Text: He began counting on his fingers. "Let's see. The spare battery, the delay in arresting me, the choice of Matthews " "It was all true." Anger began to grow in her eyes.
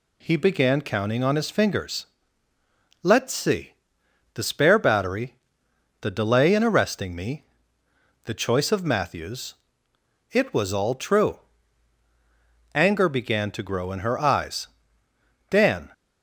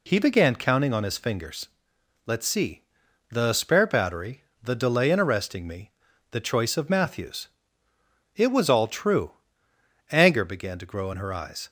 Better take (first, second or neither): second